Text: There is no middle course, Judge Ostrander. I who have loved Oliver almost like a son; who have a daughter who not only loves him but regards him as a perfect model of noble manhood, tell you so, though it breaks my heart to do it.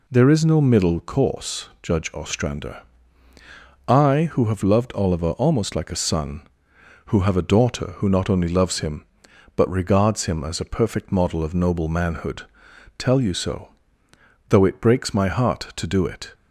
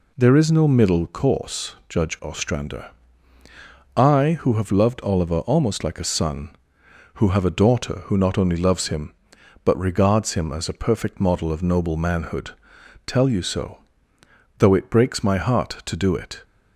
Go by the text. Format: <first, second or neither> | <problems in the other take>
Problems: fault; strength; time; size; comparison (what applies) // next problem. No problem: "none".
neither | none